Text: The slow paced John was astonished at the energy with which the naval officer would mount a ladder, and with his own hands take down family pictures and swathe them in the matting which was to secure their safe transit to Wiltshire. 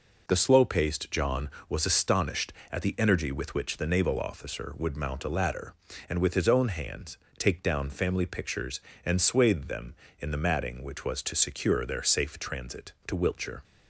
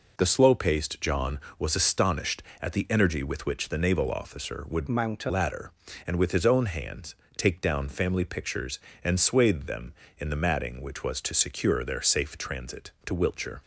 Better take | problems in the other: first | changes voice from "mount" to "a"; from 4.8 to 5.3 s; 0.5 s long // pauses between "hands" and "take"; slight; at 7.1 s; 0.20 s long; slight in the first

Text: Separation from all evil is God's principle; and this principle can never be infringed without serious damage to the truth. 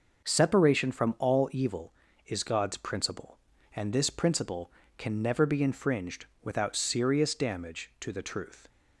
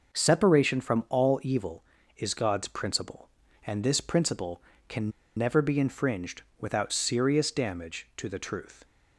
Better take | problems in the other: first | pauses between "can" and "never"; slight; at 5.1 s; 0.25 s long // pauses between "infringed" and "without"; slight; at 6.4 s; 0.16 s long; slight in the first

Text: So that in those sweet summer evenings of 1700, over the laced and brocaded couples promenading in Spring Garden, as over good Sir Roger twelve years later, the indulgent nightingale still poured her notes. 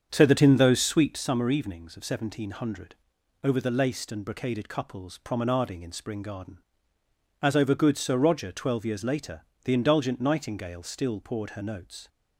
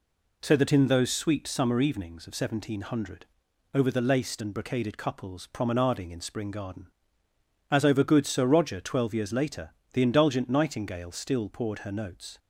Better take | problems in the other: second | starts louder than the rest; strong; until 1.2 s; 7.5 dB

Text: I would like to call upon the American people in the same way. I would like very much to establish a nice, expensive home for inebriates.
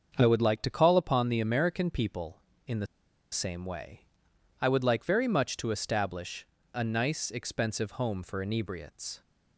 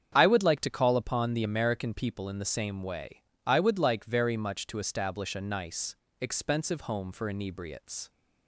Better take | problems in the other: second | starts louder than the rest; until 1.1 s; 6.5 dB; strong in the second // pauses between "the" and "same"; noticeable; at 2.8 s; 0.46 s long // pauses between "establish" and "a"; slight; at 6.4 s; 0.30 s long

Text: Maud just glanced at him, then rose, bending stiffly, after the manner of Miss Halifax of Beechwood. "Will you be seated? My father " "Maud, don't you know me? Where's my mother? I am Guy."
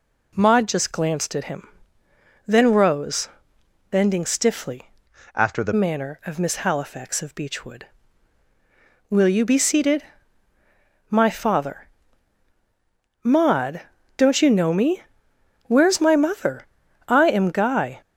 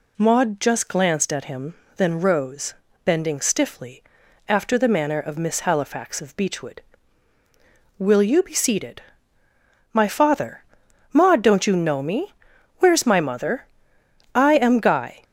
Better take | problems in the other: second | changes voice from "after" to "the"; from 5.3 to 5.7 s; 0.4 s long

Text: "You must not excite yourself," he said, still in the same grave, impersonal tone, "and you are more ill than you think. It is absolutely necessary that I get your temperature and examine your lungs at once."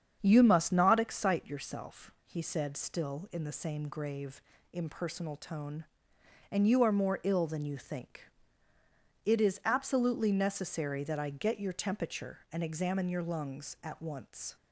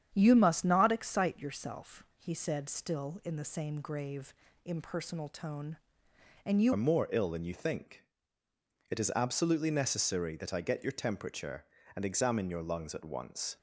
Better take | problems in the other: first | starts louder than the rest; strong; until 1.1 s; 9 dB; strong in the first // changes voice at "are"; from 6.7 s on; 6.8 s long

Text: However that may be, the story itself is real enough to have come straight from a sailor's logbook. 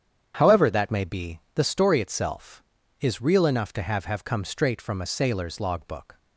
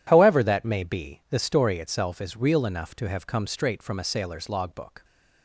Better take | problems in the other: second | starts louder than the rest; strong; until 1.5 s; 8.5 dB // says "have" twice; at 4.0 s

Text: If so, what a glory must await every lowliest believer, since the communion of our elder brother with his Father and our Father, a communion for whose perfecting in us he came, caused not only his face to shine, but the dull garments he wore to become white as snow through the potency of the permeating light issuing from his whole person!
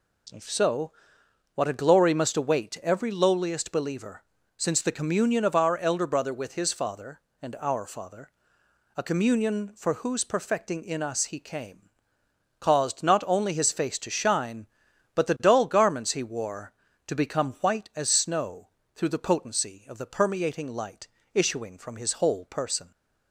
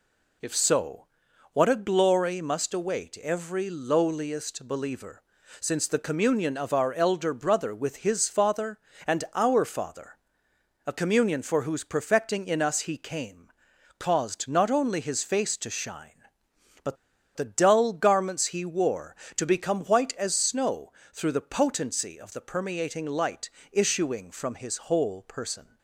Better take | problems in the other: first | pauses between "but" and "the"; at 16.9 s; 0.39 s long // pauses between "snow" and "through"; slight; at 20.9 s; 0.20 s long; slight in the first // pauses between "light" and "issuing"; slight; at 23.4 s; 0.22 s long; slight in the first

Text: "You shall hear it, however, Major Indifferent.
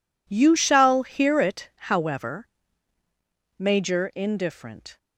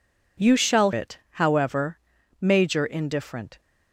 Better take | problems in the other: first | skips "hear"; at 0.9 s

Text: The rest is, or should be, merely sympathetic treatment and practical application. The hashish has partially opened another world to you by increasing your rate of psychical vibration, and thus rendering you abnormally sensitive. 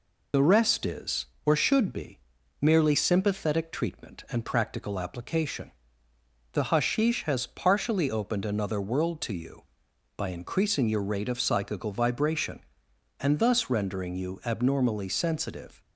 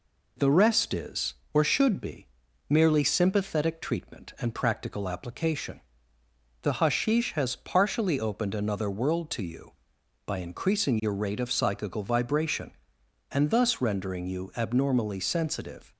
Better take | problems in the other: second | loses the start of "The"; at 0.3 s; 55 ms

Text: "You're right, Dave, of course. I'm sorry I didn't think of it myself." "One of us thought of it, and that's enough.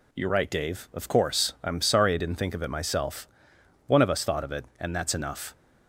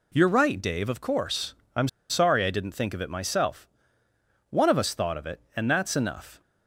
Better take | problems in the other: first | pauses between "I'm" and "sorry"; slight; at 1.8 s; 0.23 s long

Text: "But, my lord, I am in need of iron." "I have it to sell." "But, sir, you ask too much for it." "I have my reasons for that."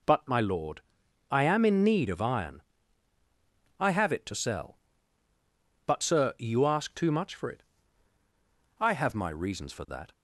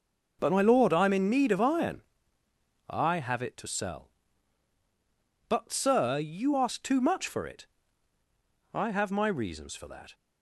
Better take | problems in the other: neither | none

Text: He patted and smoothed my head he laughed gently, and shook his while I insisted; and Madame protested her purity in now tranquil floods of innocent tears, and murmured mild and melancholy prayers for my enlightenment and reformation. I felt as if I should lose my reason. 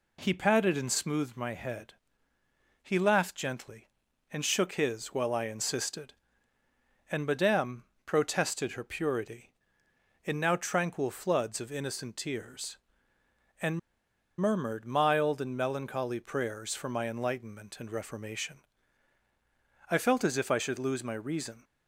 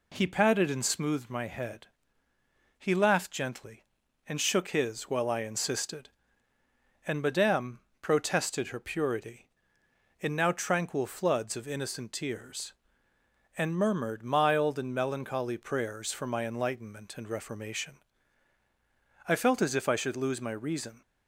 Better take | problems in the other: second | pauses between "head" and "he"; noticeable; at 1.9 s; 0.88 s long; noticeable in the second // pauses between "Madame" and "protested"; slight; at 7.8 s; 0.22 s long; slight in the second // pauses between "and" and "murmured"; noticeable; at 13.7 s; 0.59 s long

